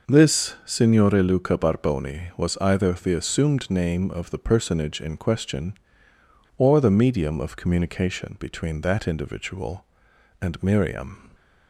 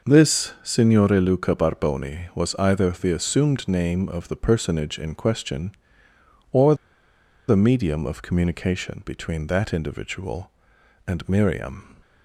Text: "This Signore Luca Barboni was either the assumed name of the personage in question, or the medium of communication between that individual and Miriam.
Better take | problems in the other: first | pauses between "or" and "the"; noticeable; at 6.7 s; 0.73 s long

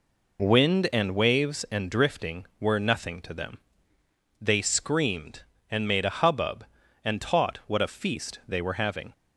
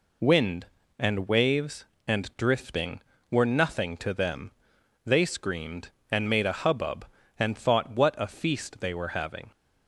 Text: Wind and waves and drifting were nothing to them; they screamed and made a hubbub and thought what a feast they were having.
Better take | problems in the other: second | says "taught" for "thought"; at 7.2 s

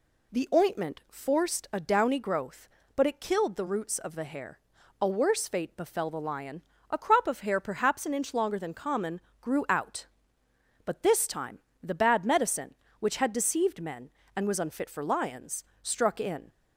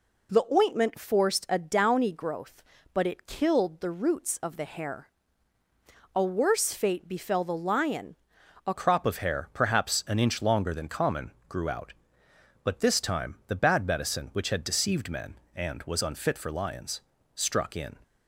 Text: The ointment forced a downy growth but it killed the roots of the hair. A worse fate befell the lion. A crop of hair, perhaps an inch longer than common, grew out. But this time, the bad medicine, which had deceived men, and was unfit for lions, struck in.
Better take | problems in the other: first | changes voice at "crop"; from 8.7 s on; 9.2 s long

